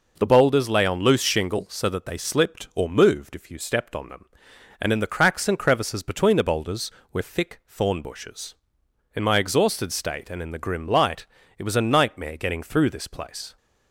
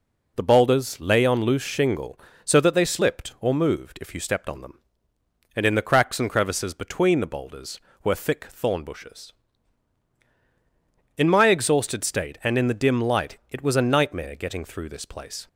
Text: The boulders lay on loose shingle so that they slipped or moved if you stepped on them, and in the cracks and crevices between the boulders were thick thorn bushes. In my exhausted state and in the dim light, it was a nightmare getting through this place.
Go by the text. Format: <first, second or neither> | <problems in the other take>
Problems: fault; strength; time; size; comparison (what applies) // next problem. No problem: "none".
second | says "grim" for "dim"; at 10.5 s